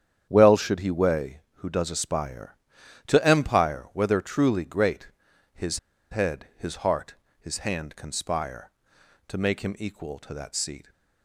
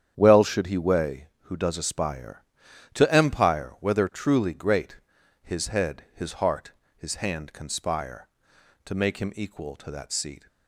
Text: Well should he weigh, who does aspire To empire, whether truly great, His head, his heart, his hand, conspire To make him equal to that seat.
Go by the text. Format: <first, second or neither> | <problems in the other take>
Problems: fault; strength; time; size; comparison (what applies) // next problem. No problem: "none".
second | starts louder than the rest; strong; until 1.3 s; 9 dB; strong in the second // pauses between "His" and "head"; slight; at 5.7 s; 0.33 s long